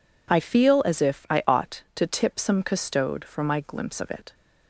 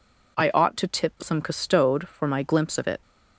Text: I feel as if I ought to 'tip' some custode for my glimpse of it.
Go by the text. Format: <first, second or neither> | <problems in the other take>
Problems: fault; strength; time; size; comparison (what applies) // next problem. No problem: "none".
first | skips "feel as if I"; at 0.5 s